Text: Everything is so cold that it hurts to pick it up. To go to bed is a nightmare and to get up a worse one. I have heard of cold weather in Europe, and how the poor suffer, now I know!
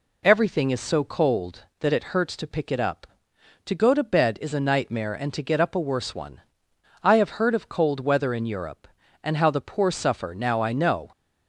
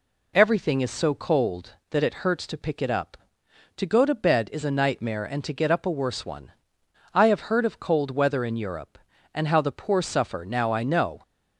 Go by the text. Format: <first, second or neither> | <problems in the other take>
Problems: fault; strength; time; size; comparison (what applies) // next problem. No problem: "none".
neither | none